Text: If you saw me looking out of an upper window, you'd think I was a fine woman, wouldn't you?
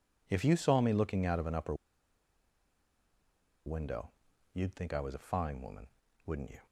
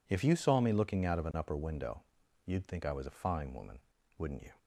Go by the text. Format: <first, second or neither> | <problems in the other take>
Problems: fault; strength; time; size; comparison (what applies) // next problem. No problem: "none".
second | pauses between "upper" and "window"; strong; at 1.7 s; 1.9 s long